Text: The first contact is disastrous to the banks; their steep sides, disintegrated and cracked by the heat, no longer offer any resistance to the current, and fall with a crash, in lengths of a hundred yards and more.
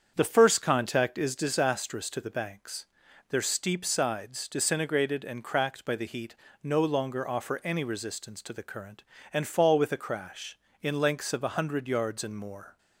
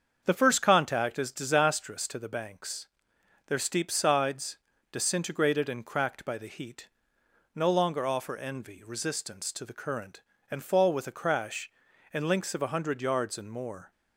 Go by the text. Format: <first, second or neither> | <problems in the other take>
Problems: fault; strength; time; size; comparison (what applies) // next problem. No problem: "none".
first | starts louder than the rest; until 1.2 s; 7 dB; strong in the first // says "envy" for "any"; at 8.3 s